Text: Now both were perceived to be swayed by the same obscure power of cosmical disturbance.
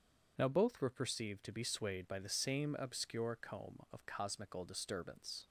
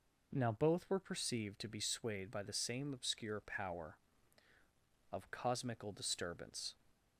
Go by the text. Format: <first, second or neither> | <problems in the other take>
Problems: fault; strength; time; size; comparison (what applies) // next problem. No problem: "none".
second | says "comb" for "power"; at 3.4 s